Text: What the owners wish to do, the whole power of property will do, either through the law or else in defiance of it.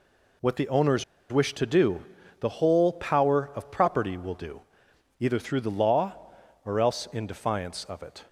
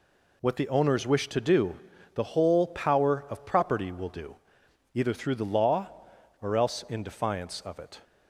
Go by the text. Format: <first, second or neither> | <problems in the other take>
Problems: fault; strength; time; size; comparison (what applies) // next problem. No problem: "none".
second | pauses between "owners" and "wish"; slight; at 1.0 s; 0.27 s long